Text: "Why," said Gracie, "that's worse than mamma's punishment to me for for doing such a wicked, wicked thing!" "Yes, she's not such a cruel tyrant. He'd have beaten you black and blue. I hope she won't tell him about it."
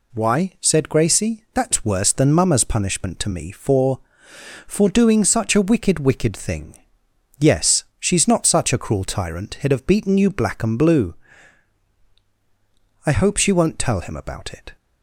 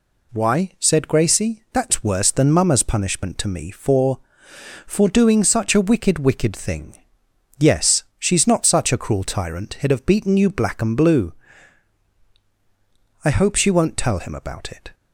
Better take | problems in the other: neither | none

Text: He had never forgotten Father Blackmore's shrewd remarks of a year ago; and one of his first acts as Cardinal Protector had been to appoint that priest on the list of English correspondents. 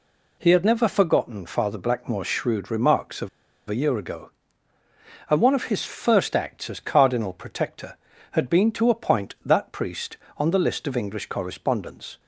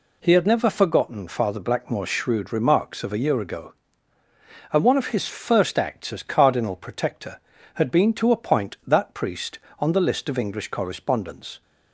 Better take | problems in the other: second | pauses between "of" and "a"; at 3.2 s; 0.38 s long

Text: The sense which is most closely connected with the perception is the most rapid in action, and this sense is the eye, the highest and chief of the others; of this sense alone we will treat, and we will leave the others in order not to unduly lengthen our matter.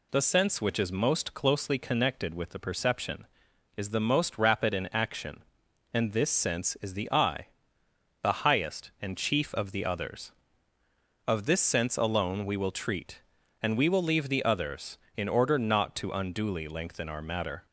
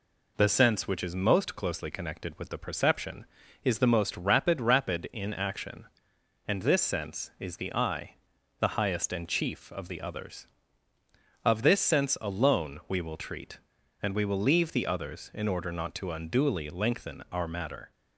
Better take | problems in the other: first | says "rapid" twice; at 4.6 s

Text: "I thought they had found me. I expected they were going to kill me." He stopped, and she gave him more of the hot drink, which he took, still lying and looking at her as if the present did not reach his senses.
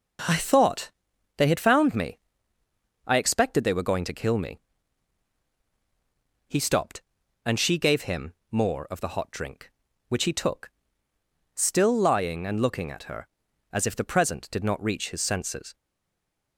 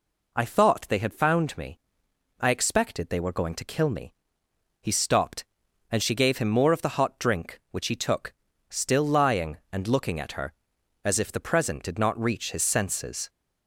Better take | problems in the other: second | pauses between "thought" and "they"; noticeable; at 0.9 s; 0.46 s long // pauses between "him" and "more"; slight; at 8.3 s; 0.16 s long // stays silent after the last word; slight; from 15.7 s on; 0.8 s long

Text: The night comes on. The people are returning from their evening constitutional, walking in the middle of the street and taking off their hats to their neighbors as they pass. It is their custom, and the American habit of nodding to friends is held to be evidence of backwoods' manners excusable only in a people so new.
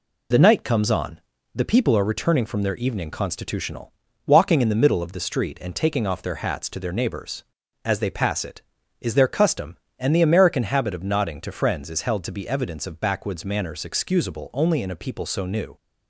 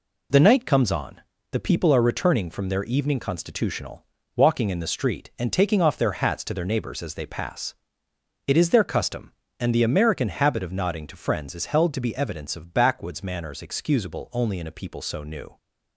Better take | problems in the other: first | skips "the middle of"; at 4.7 s

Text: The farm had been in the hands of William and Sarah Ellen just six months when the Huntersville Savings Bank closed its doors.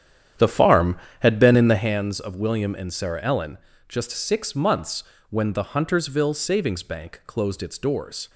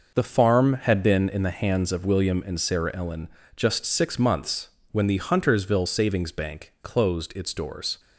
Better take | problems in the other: second | starts louder than the rest; strong; until 2.0 s; 9.5 dB // pauses between "Ellen" and "just"; slight; at 3.5 s; 0.30 s long; slight in the second // pauses between "months" and "when"; slight; at 5.0 s; 0.26 s long; slight in the second

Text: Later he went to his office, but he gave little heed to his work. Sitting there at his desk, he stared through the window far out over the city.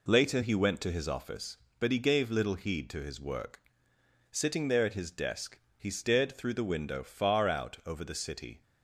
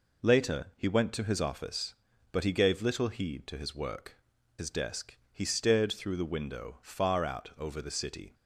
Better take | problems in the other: first | skips "Sitting there at"; at 4.3 s

